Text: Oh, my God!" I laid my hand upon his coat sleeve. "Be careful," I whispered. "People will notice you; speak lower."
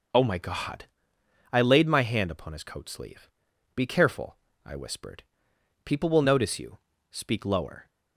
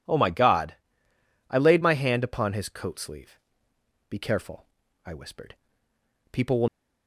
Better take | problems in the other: first | stops before "notice you speak lower"; at 6.6 s

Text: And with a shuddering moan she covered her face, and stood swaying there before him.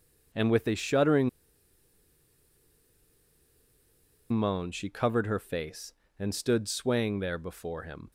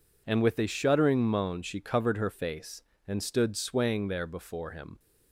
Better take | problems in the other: second | pauses between "shuddering" and "moan"; strong; at 1.2 s; 3.0 s long

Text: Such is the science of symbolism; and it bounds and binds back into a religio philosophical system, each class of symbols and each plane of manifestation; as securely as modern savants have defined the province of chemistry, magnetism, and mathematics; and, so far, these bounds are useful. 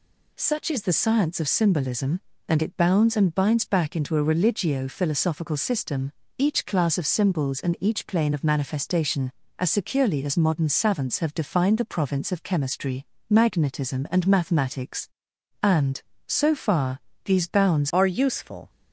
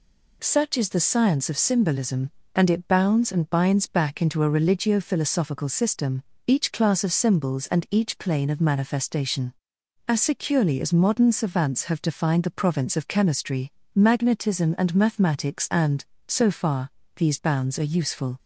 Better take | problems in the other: second | changes voice at "are"; from 17.9 s on; 0.7 s long

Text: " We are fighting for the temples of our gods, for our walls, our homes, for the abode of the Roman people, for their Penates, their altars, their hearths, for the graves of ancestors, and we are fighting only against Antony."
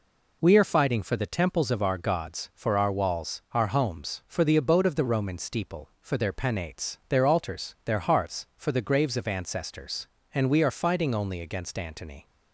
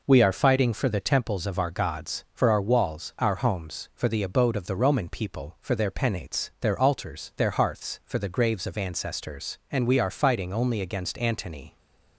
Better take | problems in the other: second | says "steeple" for "people"; at 5.3 s

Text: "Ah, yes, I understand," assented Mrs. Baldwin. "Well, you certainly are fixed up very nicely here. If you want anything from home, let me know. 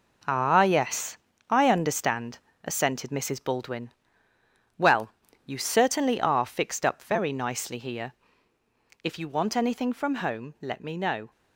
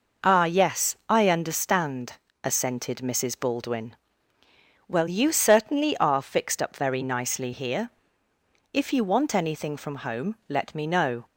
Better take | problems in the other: second | gets quieter; strong; throughout; 8 dB

